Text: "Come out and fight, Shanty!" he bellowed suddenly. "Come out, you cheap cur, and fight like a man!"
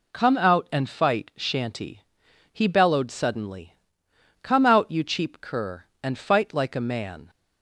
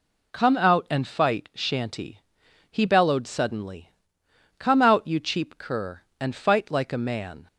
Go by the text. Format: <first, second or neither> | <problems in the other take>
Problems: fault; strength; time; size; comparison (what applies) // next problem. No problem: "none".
neither | none